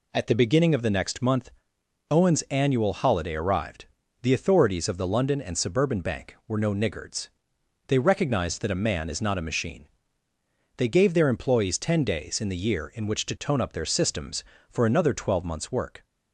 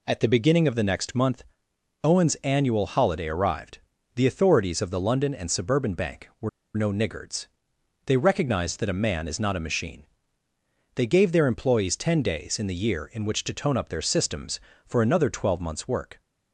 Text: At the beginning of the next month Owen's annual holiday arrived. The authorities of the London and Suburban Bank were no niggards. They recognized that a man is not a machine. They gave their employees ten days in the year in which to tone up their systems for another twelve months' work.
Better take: first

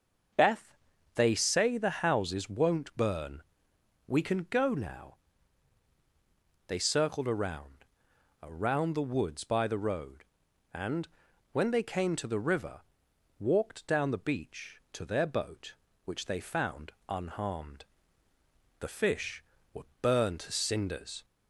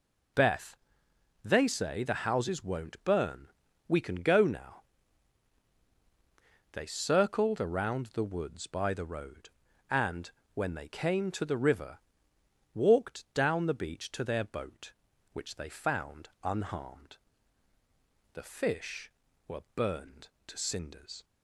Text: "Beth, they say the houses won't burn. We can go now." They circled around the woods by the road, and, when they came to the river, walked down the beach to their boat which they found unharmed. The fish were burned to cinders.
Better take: second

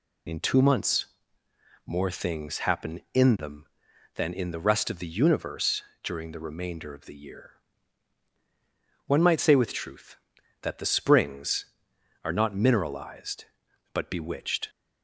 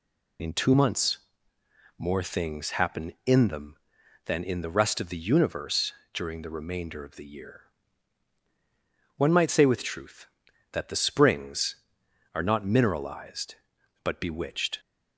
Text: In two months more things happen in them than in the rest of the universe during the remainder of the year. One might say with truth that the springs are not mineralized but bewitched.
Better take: neither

